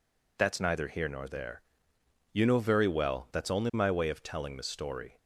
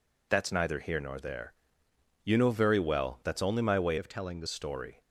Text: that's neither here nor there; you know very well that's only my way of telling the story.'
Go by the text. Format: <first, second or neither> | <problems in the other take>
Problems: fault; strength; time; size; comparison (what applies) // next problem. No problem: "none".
first | changes voice from "of" to "the"; from 3.9 to 4.4 s; 0.5 s long